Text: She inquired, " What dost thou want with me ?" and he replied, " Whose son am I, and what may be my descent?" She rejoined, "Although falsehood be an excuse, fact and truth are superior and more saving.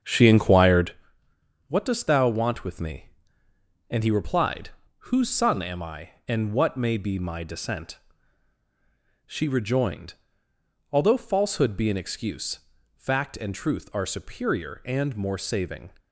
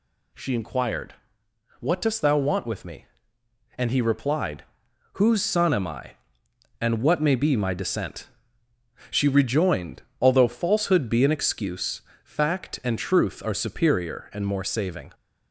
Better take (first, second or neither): second